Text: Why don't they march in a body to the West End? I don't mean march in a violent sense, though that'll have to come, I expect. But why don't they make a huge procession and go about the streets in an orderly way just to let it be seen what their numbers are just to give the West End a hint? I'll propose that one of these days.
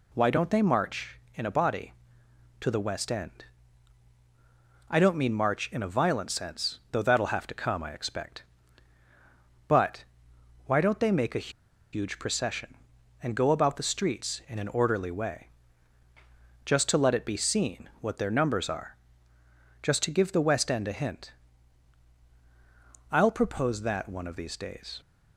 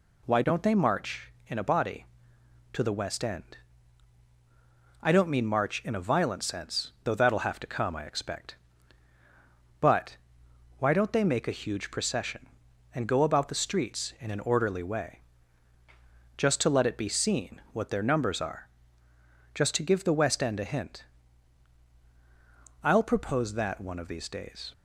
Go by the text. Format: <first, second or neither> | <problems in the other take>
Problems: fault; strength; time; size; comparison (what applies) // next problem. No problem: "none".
second | pauses between "But" and "why"; noticeable; at 10.0 s; 0.62 s long; noticeable in the second // pauses between "a" and "huge"; at 11.4 s; 0.43 s long // pauses between "way" and "just"; at 15.4 s; 1.2 s long; also in the second // pauses between "are" and "just"; noticeable; at 18.9 s; 0.86 s long; noticeable in the second